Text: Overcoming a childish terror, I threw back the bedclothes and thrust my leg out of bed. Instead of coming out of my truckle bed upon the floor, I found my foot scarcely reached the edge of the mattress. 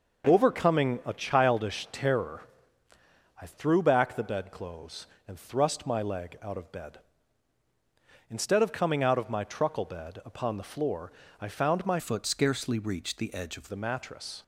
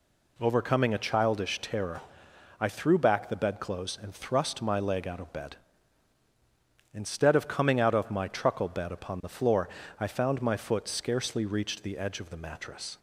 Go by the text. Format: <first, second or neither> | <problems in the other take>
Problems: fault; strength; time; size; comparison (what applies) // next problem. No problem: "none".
second | changes voice from "foot" to "of"; from 11.9 to 13.6 s; 1.7 s long